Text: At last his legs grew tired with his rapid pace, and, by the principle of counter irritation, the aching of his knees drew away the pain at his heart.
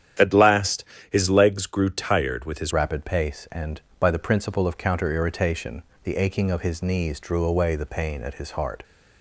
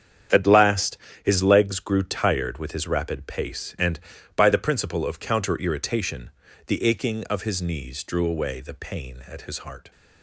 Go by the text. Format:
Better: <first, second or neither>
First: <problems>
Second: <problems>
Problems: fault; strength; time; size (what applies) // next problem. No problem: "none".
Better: second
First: starts louder than the rest; strong; until 1.4 s; 10 dB // pauses between "last" and "his"; slight; at 0.8 s; 0.28 s long // changes voice at "rapid"; from 2.7 s on; 6.1 s long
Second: starts louder than the rest; strong; until 1.6 s; 8.5 dB // pauses between "last" and "his"; slight; at 0.9 s; 0.28 s long